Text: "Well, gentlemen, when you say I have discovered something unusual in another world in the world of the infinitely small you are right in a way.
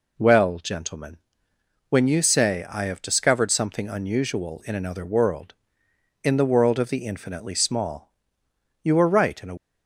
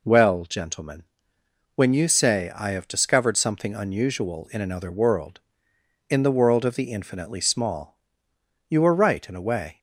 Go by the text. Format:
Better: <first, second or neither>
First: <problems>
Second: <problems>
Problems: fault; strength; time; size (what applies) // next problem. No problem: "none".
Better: second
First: pauses between "small" and "you"; noticeable; at 8.1 s; 0.70 s long // stops before "way"; at 9.5 s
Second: pauses between "small" and "you"; noticeable; at 7.9 s; 0.70 s long